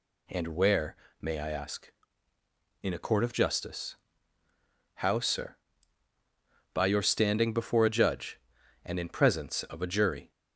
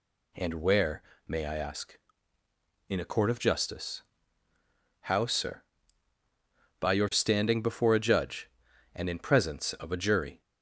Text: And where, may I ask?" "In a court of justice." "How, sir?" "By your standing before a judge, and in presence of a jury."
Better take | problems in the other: neither | none

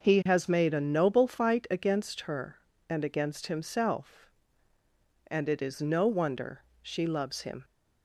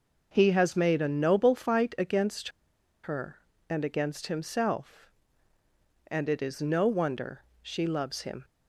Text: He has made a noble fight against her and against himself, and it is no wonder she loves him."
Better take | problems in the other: first | pauses between "against" and "her"; noticeable; at 2.4 s; 0.55 s long // pauses between "wonder" and "she"; slight; at 7.4 s; 0.22 s long; slight in the first

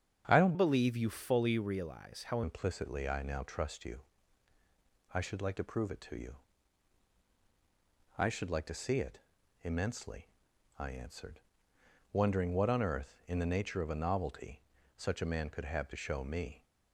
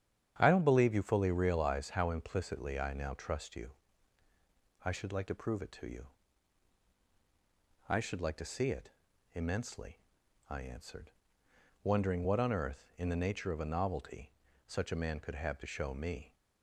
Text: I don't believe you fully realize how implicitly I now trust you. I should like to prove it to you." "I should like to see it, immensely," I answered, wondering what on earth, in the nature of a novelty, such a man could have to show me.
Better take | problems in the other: second | starts louder than the rest; strong; until 1.3 s; 8 dB; strong in the second // changes voice from "believe" to "how"; from 0.5 to 2.4 s; 1.9 s long

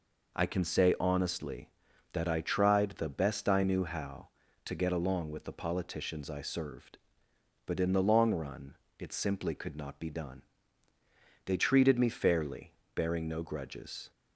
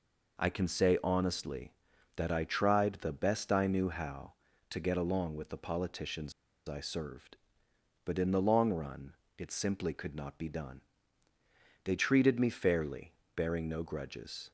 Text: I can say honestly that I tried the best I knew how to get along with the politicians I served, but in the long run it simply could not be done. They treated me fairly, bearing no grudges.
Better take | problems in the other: first | pauses between "politicians" and "I"; slight; at 6.3 s; 0.34 s long // pauses between "run" and "it"; slight; at 9.1 s; 0.22 s long; slight in the first

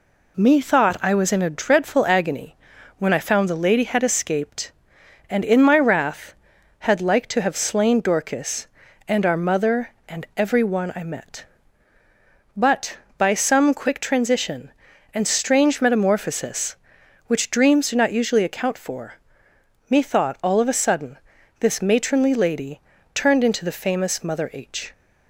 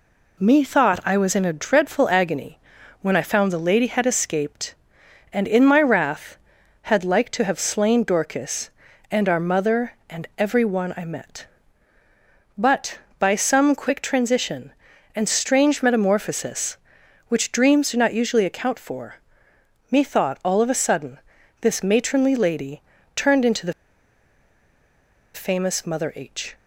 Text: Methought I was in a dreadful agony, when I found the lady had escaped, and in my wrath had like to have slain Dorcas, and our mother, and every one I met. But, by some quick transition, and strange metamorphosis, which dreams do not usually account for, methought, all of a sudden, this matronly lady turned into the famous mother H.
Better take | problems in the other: first | pauses between "lady" and "turned"; slight; at 22.8 s; 0.34 s long; slight in the first // pauses between "the" and "famous"; strong; at 23.7 s; 1.6 s long

